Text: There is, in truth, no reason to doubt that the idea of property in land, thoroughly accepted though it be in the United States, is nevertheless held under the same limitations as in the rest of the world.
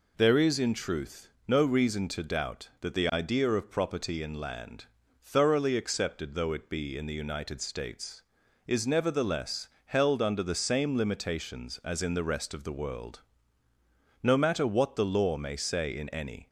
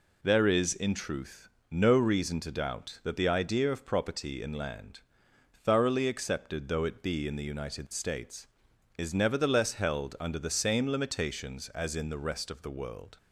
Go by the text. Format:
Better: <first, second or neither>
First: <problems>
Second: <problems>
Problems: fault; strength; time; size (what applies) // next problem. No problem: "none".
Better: second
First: pauses between "nevertheless" and "held"; slight; at 9.6 s; 0.20 s long // goes on to say "No matter what the law may say in any"; strong; from 14.2 s on; 2.2 s long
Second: none